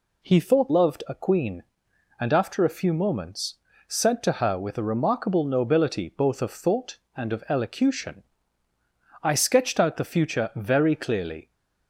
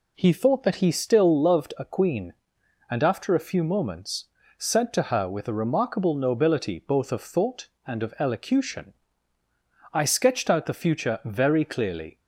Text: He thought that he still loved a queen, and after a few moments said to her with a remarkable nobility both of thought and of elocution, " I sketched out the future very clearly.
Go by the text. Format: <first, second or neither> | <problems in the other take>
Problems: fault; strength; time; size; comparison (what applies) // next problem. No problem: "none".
second | skips "that he still"; at 0.7 s // pauses between "moments" and "said"; slight; at 3.5 s; 0.32 s long; slight in the second